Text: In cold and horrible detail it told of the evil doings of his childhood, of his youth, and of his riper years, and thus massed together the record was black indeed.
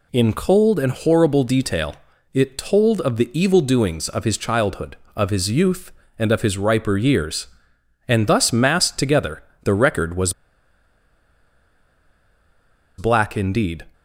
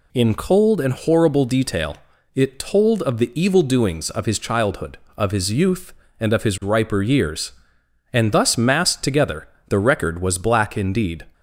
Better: second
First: pauses between "detail" and "it"; at 1.9 s; 0.38 s long // pauses between "together" and "the"; slight; at 9.4 s; 0.22 s long // pauses between "was" and "black"; strong; at 10.3 s; 2.6 s long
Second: pauses between "detail" and "it"; at 1.9 s; 0.38 s long // pauses between "together" and "the"; slight; at 9.4 s; 0.22 s long

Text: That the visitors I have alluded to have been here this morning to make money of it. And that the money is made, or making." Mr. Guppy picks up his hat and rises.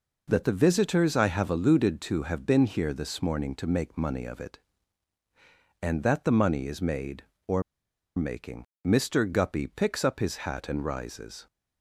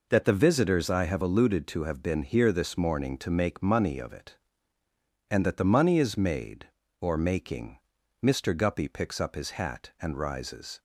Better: second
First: pauses between "or" and "making"; noticeable; at 7.6 s; 0.54 s long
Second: none

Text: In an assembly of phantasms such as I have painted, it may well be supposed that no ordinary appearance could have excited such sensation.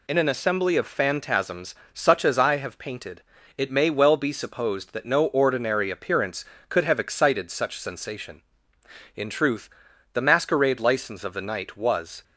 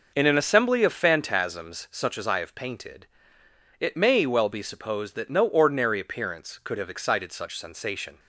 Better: second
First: pauses between "phantasms" and "such"; slight; at 1.7 s; 0.18 s long // goes on to say "In truth the masquerade license of the night was"; strong; from 9.1 s on; 3.0 s long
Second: none

